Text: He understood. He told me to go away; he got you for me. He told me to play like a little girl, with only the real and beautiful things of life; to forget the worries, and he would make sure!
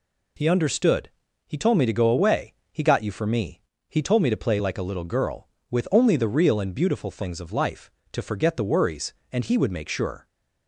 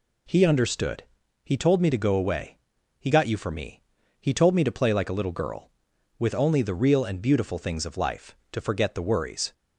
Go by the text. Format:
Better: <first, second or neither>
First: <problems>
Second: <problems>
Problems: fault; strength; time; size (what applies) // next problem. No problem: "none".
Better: first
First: none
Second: stops before "and he would make sure"; at 9.5 s